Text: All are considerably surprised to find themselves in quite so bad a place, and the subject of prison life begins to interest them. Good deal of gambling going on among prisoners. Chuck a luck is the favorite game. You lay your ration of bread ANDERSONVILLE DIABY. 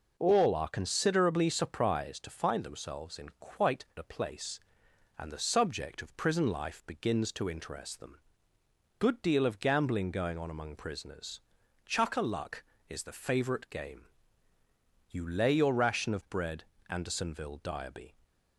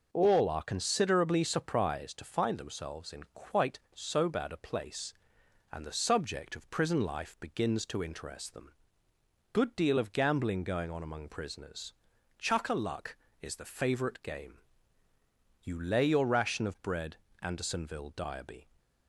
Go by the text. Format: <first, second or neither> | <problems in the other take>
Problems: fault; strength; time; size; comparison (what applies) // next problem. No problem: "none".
second | skips "so bad"; at 3.9 s // pauses between "bread" and "ANDERSONVILLE"; slight; at 16.6 s; 0.26 s long; slight in the second